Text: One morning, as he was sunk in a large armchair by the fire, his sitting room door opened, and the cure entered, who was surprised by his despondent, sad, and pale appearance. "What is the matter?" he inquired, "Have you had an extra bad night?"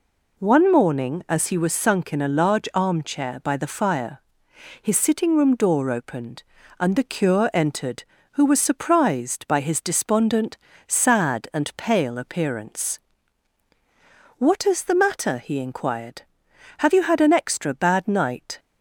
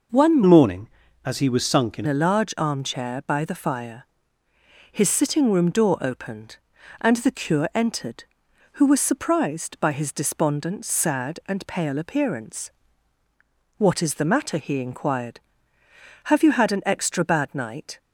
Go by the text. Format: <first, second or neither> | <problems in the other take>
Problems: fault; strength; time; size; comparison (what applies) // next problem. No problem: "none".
first | changes voice from "morning" to "in"; from 0.4 to 2.0 s; 1.6 s long